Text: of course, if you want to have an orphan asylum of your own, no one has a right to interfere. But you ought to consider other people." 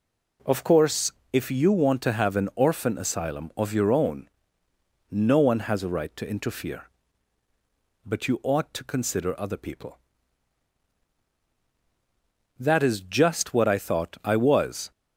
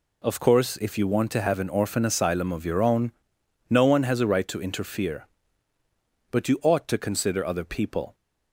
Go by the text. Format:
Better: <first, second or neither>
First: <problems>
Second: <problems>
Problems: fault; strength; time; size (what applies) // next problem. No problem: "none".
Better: second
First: goes on to say "That is just what I thought I was"; strong; from 12.5 s on; 2.3 s long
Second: none